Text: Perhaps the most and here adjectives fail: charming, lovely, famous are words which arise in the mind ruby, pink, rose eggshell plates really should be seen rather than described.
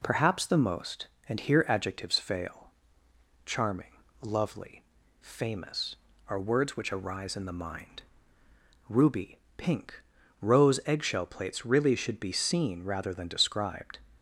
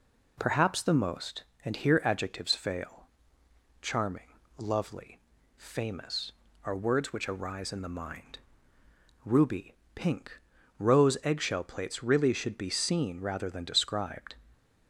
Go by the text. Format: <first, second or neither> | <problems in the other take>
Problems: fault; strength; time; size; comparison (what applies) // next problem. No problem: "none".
neither | pauses between "mind" and "ruby"; noticeable; the same in both